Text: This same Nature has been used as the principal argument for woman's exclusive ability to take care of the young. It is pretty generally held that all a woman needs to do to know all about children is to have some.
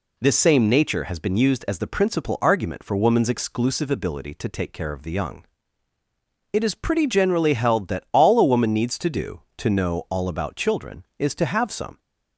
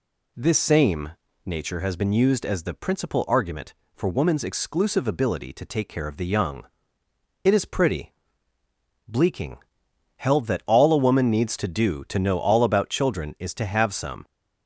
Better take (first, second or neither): first